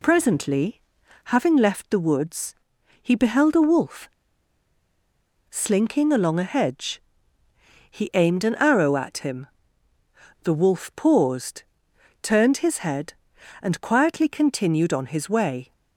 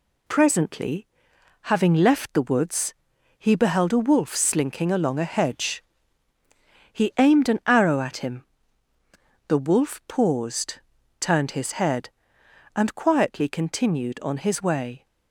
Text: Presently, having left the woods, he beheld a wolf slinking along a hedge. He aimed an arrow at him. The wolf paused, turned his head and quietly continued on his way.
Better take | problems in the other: second | pauses between "wolf" and "slinking"; strong; at 4.0 s; 1.4 s long

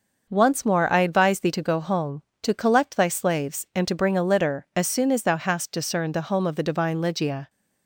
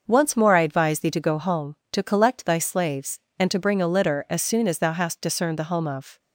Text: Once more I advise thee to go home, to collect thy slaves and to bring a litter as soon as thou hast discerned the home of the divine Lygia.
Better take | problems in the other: first | starts louder than the rest; until 1.0 s; 6 dB; noticeable in the first // stops before "the divine Lygia"; at 6.1 s

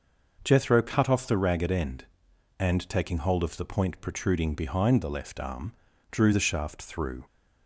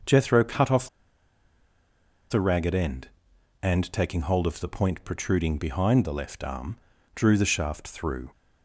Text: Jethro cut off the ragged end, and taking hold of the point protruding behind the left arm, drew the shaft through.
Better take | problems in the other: first | starts louder than the rest; noticeable; until 2.4 s; 6 dB // pauses between "off" and "the"; strong; at 0.8 s; 1.4 s long

